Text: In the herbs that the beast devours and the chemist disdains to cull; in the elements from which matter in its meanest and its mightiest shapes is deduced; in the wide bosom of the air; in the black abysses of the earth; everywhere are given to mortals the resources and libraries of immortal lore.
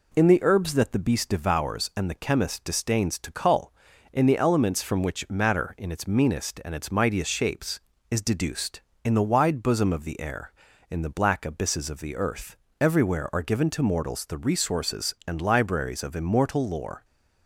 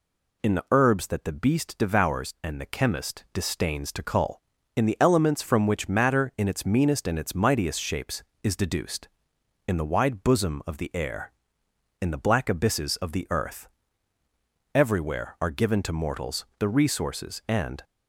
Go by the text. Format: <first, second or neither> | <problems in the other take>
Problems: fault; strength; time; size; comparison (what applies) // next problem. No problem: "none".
first | stops before "libraries of immortal lore"; at 17.8 s